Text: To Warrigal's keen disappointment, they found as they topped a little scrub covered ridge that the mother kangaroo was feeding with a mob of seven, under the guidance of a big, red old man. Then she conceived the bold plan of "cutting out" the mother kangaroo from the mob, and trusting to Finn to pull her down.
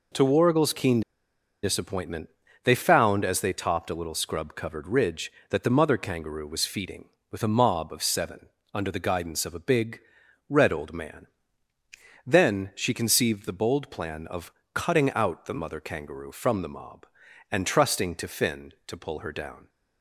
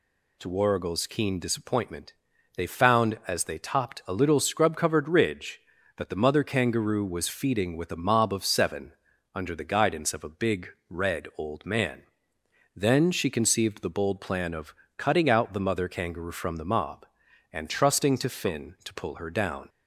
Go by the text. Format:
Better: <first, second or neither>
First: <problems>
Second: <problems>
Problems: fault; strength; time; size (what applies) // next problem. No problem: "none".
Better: second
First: pauses between "keen" and "disappointment"; noticeable; at 1.0 s; 0.62 s long // pauses between "of" and "cutting"; slight; at 14.5 s; 0.22 s long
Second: pauses between "of" and "cutting"; slight; at 14.7 s; 0.24 s long